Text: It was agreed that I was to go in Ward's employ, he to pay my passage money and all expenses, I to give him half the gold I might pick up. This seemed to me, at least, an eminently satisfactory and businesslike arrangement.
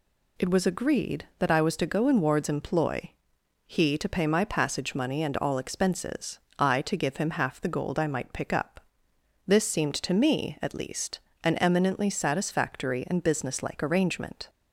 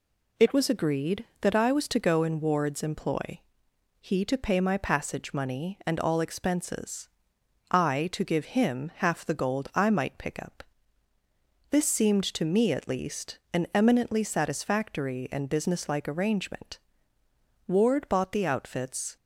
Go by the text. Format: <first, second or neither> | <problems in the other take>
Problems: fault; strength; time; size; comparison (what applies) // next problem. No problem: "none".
first | goes on to say "Ward bought the outfits"; from 17.6 s on; 1.4 s long